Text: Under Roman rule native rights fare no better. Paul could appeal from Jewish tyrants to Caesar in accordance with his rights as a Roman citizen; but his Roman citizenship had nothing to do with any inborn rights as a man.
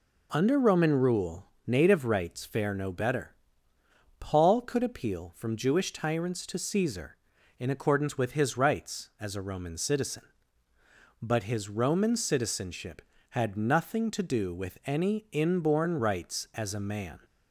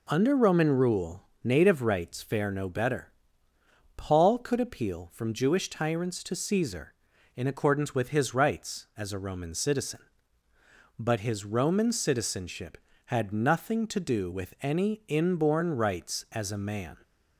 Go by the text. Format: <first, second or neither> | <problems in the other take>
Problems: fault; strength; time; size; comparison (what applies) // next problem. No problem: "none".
neither | pauses between "rule" and "native"; slight; the same in both